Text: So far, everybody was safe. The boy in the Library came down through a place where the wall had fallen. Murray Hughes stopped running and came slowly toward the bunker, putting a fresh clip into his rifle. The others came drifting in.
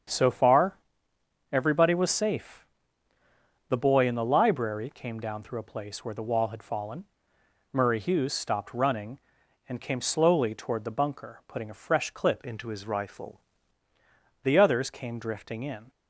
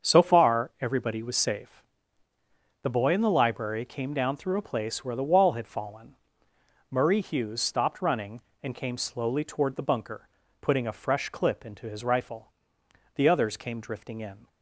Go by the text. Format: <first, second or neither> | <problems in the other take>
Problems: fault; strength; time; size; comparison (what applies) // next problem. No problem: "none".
second | starts louder than the rest; strong; until 1.8 s; 7.5 dB; also in the second // changes voice from "into" to "rifle"; from 12.4 to 13.3 s; 0.9 s long